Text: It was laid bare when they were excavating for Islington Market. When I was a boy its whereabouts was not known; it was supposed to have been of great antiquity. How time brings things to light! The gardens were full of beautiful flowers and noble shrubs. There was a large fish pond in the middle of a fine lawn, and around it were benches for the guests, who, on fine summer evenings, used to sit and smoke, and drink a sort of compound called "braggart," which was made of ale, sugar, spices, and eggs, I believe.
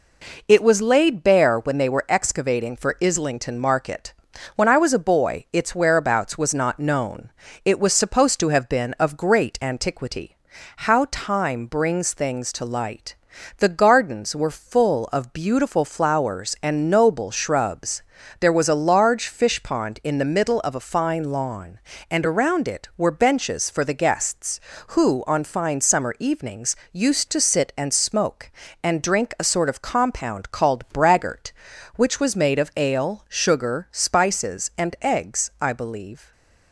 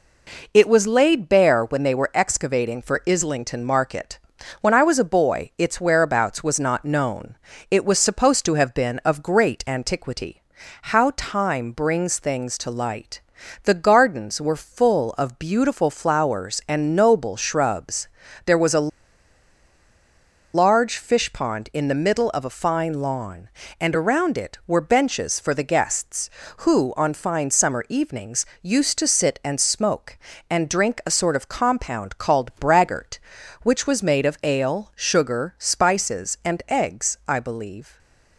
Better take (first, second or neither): first